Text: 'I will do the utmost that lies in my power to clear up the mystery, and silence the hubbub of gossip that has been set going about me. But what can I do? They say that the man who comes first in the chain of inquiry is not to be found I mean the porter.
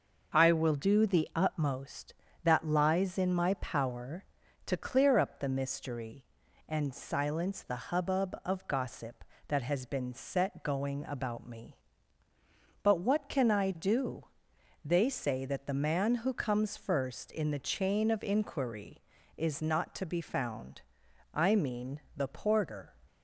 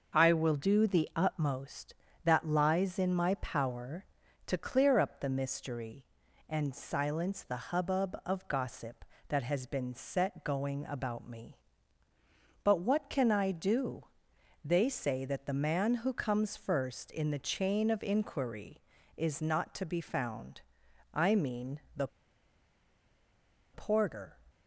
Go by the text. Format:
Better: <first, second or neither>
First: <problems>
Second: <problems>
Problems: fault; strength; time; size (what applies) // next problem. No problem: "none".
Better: first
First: pauses between "found" and "I"; noticeable; at 20.8 s; 0.52 s long // pauses between "mean" and "the"; slight; at 21.9 s; 0.16 s long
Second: pauses between "found" and "I"; noticeable; at 20.6 s; 0.52 s long // pauses between "mean" and "the"; slight; at 21.7 s; 0.16 s long // pauses between "the" and "porter"; strong; at 22.0 s; 1.6 s long